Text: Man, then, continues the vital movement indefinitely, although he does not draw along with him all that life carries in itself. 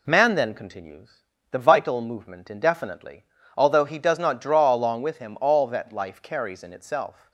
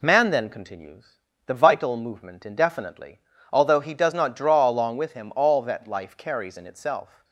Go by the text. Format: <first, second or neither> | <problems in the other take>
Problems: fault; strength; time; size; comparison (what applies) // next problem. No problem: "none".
neither | pauses between "continues" and "the"; slight; the same in both